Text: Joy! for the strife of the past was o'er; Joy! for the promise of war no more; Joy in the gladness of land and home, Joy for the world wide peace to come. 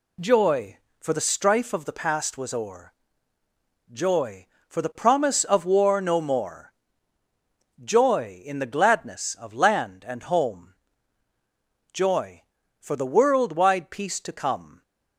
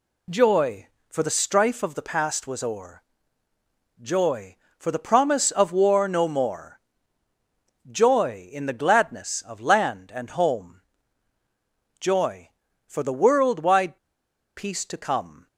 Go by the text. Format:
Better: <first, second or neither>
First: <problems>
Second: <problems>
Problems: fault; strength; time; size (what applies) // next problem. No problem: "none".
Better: first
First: none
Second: pauses between "wide" and "peace"; noticeable; at 13.9 s; 0.59 s long